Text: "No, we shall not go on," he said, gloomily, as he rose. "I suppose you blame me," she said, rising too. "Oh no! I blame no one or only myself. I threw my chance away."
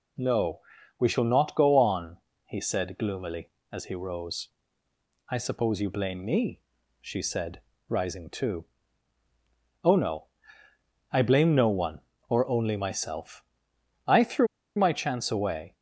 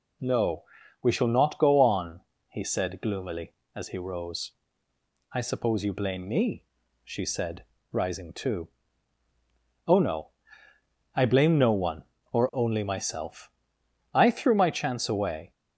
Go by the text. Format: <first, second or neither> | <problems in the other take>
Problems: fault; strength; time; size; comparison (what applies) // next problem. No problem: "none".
second | pauses between "threw" and "my"; slight; at 14.4 s; 0.30 s long